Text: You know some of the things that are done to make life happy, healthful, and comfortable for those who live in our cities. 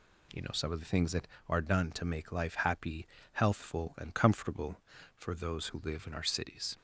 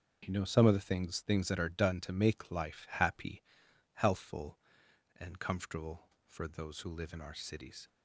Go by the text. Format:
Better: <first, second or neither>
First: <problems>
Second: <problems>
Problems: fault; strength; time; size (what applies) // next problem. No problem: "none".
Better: first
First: none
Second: starts louder than the rest; until 1.2 s; 6.5 dB // says "things" twice; at 1.1 s